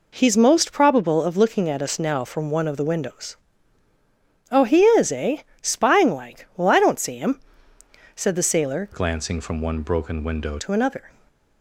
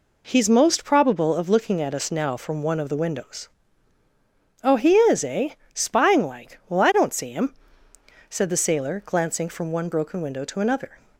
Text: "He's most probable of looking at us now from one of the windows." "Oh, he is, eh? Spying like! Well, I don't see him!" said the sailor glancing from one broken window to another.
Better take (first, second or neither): second